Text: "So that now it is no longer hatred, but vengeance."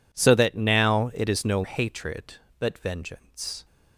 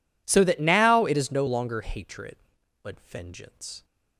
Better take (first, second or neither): second